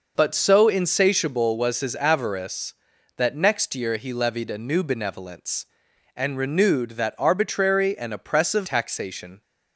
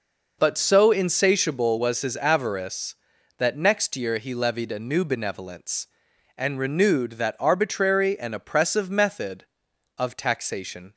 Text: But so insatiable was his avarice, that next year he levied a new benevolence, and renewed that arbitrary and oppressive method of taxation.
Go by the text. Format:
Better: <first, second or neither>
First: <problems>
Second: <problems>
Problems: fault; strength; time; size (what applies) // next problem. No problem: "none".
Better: second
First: skips "method of"; at 8.6 s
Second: none